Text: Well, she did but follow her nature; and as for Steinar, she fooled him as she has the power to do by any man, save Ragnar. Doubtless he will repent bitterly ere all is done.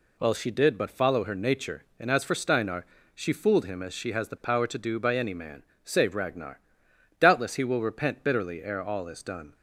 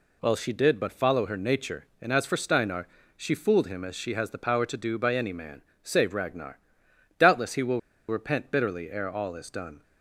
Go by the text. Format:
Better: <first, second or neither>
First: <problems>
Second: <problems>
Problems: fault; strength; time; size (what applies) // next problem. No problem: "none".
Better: first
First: none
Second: pauses between "will" and "repent"; slight; at 7.7 s; 0.29 s long